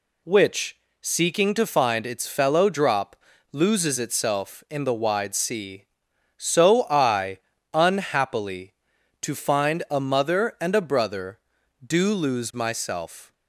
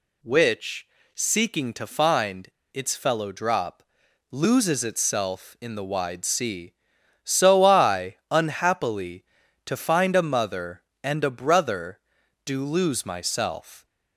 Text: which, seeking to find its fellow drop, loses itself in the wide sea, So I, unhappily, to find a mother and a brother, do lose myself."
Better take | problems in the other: first | pauses between "find" and "its"; slight; at 2.4 s; 0.24 s long

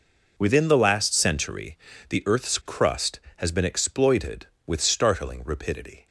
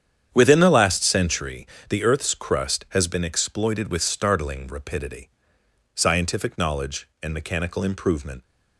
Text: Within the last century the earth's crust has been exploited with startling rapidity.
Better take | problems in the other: first | starts louder than the rest; strong; until 1.3 s; 8.5 dB // pauses between "century" and "the"; slight; at 1.6 s; 0.22 s long; slight in the first // goes on to say "Scientific knowledge and mechanical improvement"; strong; from 5.9 s on; 2.4 s long

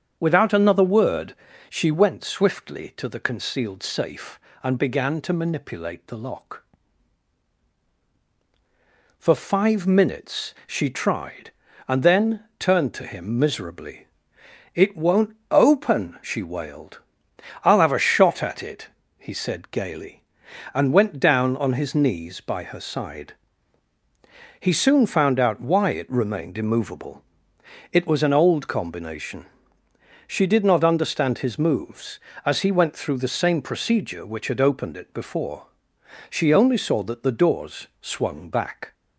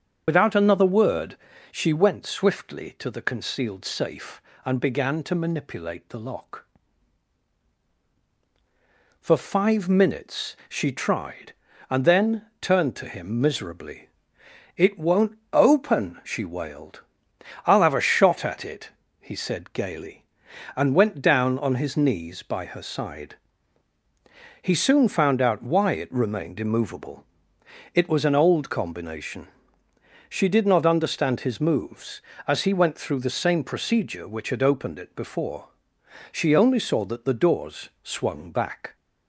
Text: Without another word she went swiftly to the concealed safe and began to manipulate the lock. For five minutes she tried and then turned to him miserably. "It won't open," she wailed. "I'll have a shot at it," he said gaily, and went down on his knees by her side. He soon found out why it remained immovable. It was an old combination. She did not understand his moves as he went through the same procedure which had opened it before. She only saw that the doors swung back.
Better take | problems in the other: first | loses the start of "Without"; at 0.2 s; 65 ms // starts louder than the rest; strong; until 1.2 s; 7.5 dB; strong in the first // pauses between "word" and "she"; slight; at 1.3 s; 0.34 s long; slight in the first // pauses between "then" and "turned"; slight; at 12.4 s; 0.16 s long; slight in the first // pauses between "won't" and "open"; slight; at 15.3 s; 0.16 s long; slight in the first

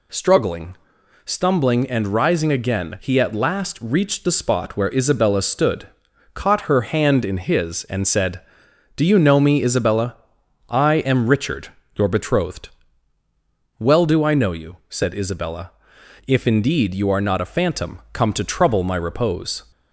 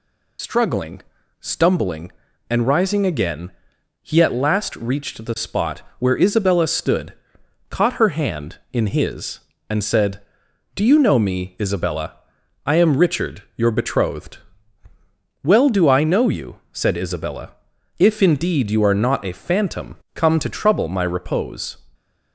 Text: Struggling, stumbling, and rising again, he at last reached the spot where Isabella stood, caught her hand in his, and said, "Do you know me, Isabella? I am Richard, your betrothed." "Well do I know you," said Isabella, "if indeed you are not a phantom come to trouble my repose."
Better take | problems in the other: first | loses the start of "Struggling"; at 0.3 s; 80 ms // pauses between "spot" and "where"; slight; at 5.8 s; 0.18 s long // pauses between "phantom" and "come"; slight; at 19.9 s; 0.16 s long

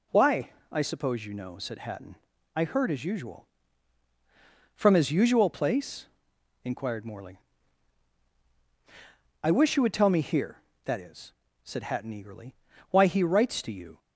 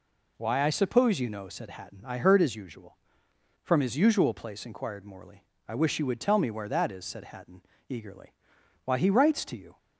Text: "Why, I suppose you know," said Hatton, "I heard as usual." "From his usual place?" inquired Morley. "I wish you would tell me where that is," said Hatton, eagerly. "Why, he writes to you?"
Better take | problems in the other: second | says "here" for "where"; at 10.2 s

